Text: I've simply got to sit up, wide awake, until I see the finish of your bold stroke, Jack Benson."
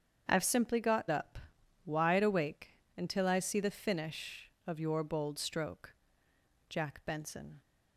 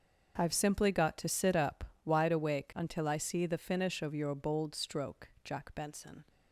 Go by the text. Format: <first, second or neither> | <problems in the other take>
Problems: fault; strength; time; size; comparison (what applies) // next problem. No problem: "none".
second | starts louder than the rest; strong; until 1.3 s; 8 dB; also in the second // skips "to sit"; at 1.0 s